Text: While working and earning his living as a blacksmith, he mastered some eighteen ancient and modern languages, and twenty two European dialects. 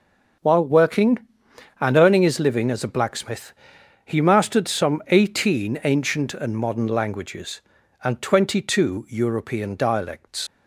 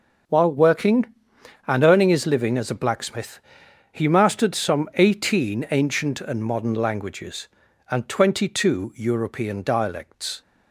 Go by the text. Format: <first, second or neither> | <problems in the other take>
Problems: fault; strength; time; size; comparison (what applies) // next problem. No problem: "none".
second | starts louder than the rest; noticeable; until 2.0 s; 6 dB // leaves "dialects" unfinished; at 10.4 s; 75 ms